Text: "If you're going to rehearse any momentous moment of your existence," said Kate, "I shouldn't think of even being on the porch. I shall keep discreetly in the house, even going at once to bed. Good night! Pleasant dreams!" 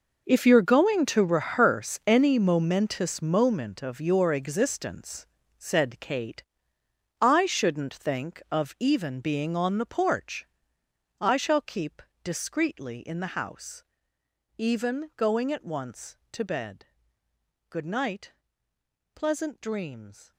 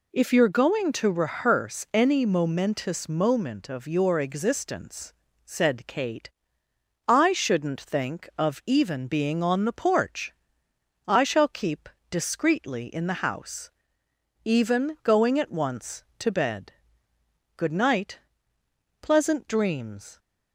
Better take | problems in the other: second | gets quieter; strong; throughout; 15 dB // pauses between "keep" and "discreetly"; slight; at 12.0 s; 0.20 s long; slight in the second

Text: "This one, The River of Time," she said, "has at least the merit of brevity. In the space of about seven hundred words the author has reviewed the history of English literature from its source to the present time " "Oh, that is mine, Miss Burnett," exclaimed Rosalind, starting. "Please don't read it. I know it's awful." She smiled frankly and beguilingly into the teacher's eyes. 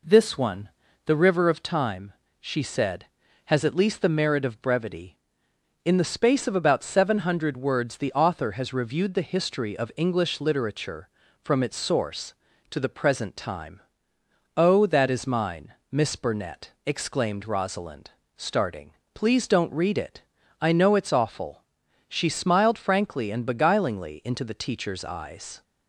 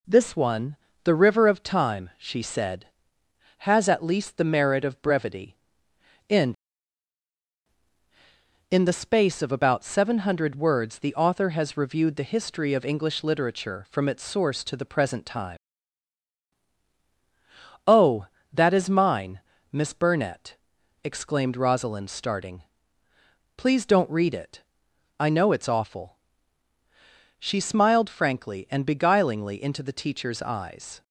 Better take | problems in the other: first | says "In" twice; at 8.6 s

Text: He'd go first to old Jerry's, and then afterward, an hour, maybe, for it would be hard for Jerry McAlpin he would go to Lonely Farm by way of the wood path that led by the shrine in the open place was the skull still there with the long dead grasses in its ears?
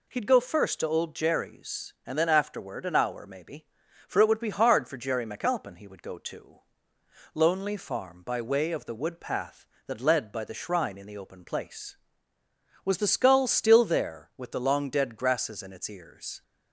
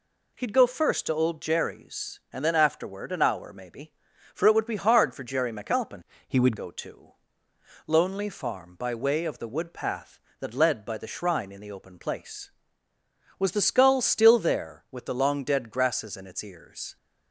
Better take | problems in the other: first | changes voice from "he" to "would"; from 6.2 to 6.5 s; 0.3 s long // pauses between "to" and "Lonely"; noticeable; at 7.1 s; 0.74 s long; noticeable in the first

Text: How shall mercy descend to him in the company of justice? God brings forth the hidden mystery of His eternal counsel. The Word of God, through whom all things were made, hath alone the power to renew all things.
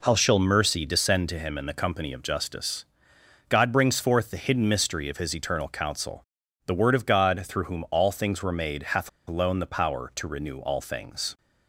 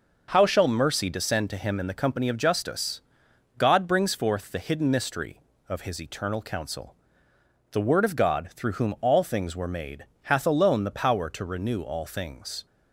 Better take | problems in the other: second | pauses between "hath" and "alone"; slight; at 9.0 s; 0.19 s long

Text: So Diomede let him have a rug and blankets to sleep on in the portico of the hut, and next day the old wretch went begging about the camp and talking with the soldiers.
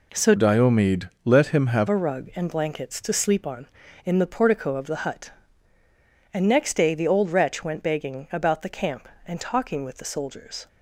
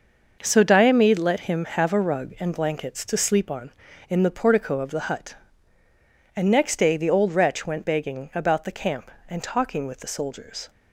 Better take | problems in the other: second | changes voice from "Diomede" to "have"; from 0.3 to 1.8 s; 1.5 s long // pauses between "Diomede" and "let"; slight; at 1.0 s; 0.16 s long

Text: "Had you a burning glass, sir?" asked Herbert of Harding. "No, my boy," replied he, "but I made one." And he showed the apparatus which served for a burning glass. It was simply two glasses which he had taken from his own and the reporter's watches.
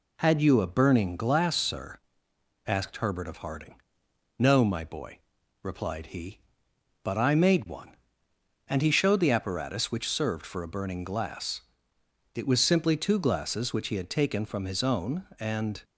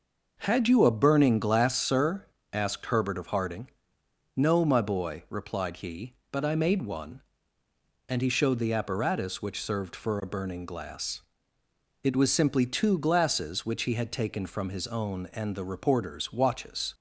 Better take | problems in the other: second | stops before "the reporter's watches"; at 15.8 s

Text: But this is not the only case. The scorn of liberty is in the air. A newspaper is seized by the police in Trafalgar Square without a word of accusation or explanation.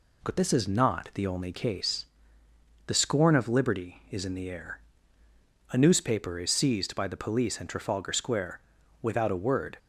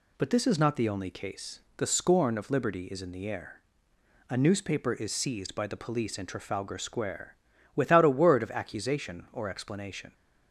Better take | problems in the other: second | pauses between "Square" and "without"; at 8.5 s; 0.42 s long; also in the second // stops before "of accusation or explanation"; at 9.7 s

